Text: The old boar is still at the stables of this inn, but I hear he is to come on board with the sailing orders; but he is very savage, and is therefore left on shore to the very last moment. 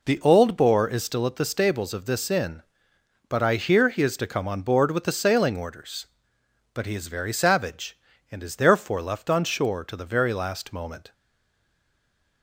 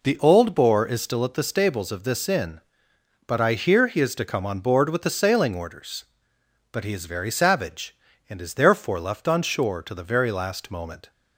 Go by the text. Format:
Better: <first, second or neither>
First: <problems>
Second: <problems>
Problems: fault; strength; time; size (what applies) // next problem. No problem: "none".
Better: second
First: stays silent after the last word; noticeable; from 11.1 s on; 1.3 s long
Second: none